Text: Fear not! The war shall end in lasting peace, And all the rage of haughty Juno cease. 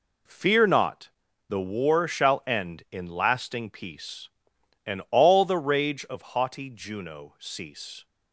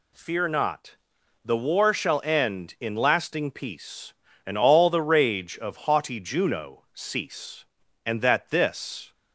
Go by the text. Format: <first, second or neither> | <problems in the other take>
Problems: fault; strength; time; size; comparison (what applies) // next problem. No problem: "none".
first | goes on to say "And that this"; noticeable; from 8.0 s on; 1.0 s long